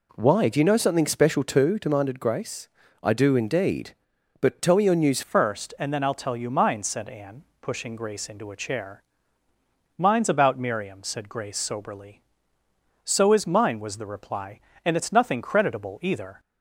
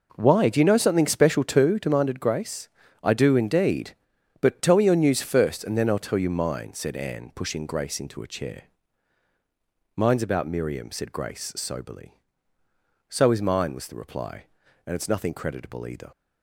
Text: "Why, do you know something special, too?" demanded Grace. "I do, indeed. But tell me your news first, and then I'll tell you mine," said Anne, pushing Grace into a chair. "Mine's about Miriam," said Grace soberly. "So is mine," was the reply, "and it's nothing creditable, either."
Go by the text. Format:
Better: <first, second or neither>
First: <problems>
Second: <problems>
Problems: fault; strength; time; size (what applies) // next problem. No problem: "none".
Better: second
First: changes voice at "first"; from 5.2 s on; 11.1 s long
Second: none